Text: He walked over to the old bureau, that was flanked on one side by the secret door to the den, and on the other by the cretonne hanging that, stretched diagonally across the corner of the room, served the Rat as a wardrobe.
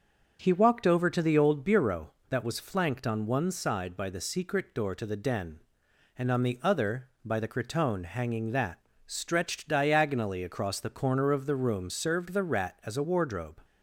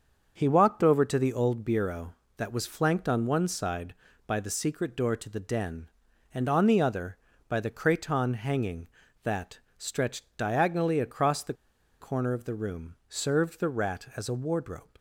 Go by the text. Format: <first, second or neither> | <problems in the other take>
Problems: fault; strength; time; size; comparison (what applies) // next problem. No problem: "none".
first | starts louder than the rest; until 1.3 s; 6.5 dB; also in the first // pauses between "the" and "corner"; noticeable; at 11.5 s; 0.46 s long